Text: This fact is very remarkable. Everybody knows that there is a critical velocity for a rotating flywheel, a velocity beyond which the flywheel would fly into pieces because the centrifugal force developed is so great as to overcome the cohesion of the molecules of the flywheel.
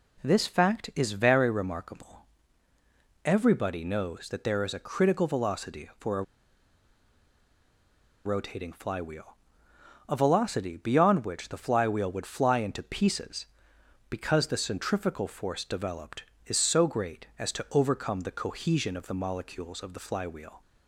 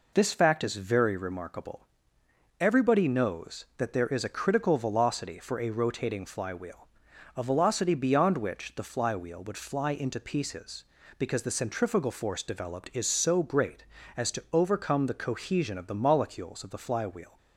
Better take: second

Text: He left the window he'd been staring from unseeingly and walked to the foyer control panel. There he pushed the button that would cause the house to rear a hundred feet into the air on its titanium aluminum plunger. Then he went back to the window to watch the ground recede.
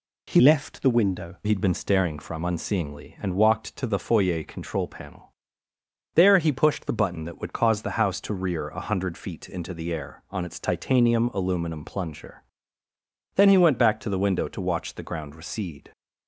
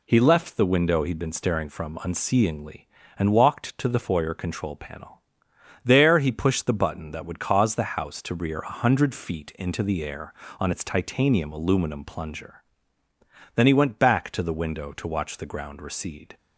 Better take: second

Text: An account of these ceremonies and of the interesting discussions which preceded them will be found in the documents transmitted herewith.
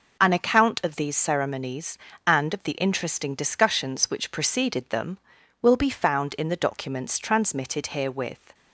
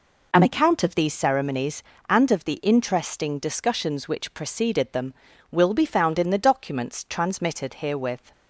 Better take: neither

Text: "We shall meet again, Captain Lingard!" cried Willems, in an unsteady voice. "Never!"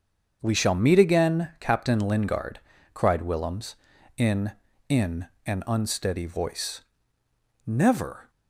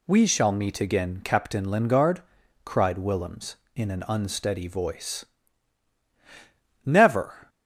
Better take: second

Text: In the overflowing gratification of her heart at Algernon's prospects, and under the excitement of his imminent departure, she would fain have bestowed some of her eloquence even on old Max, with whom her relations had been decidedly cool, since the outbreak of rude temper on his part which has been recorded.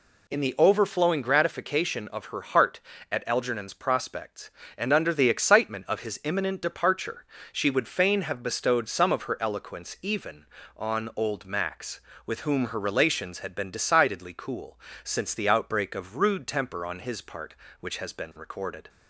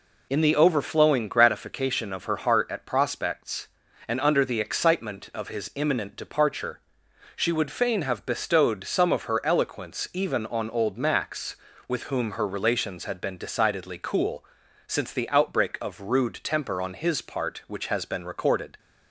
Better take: first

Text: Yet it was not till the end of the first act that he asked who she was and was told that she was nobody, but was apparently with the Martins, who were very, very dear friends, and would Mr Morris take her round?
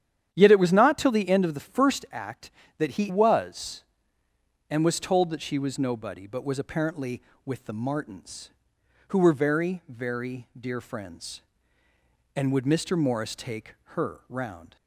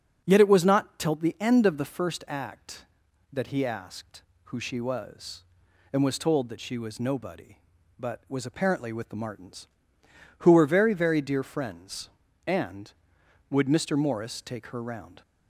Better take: second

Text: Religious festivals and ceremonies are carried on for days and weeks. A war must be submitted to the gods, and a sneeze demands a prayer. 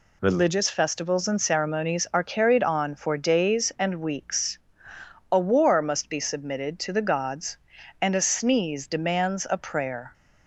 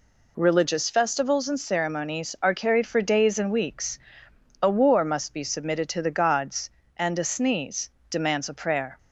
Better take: first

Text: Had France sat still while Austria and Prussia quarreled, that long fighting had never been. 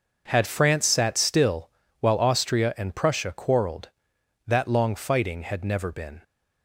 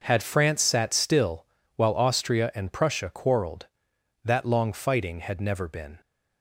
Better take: neither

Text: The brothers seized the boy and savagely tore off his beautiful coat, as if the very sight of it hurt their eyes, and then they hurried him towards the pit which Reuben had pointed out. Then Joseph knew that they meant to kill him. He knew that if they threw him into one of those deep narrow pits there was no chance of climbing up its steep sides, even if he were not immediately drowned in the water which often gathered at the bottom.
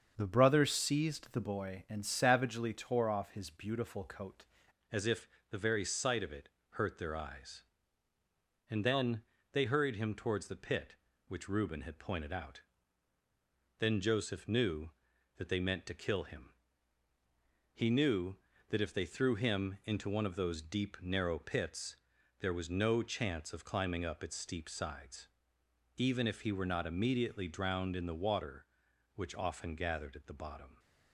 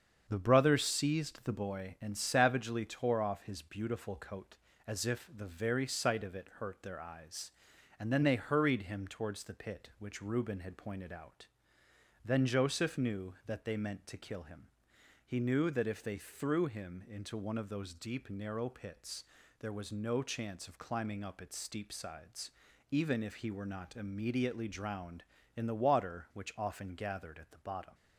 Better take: second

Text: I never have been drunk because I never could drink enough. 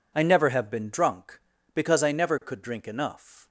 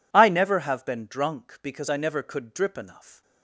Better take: first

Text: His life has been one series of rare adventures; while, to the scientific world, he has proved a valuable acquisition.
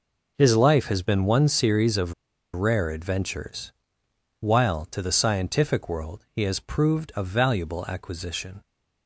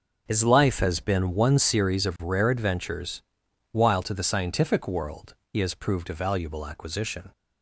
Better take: second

